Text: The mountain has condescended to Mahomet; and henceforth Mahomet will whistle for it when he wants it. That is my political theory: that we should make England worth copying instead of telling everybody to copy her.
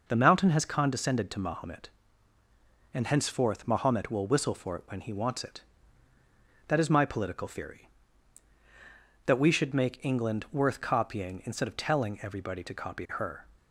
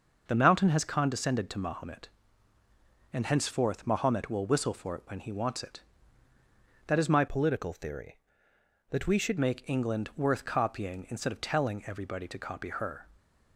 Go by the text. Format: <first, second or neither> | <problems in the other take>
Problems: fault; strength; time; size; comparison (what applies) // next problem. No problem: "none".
first | starts louder than the rest; noticeable; until 1.2 s; 6 dB // changes voice from "political" to "should"; from 7.2 to 9.3 s; 2.1 s long